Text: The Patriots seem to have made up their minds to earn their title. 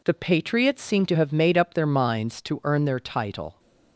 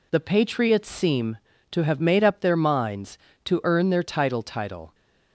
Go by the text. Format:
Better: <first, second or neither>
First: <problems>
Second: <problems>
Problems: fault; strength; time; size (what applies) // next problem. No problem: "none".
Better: first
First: none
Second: says "title" twice; at 4.4 s